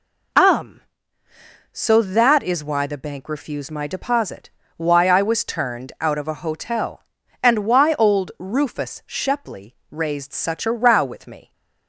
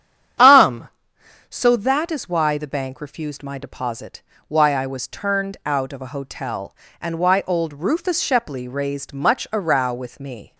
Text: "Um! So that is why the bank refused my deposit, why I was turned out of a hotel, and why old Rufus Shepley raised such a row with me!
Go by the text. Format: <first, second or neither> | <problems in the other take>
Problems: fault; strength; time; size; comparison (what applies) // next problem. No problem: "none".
first | starts louder than the rest; strong; until 2.0 s; 9.5 dB // says "much" for "such"; at 9.1 s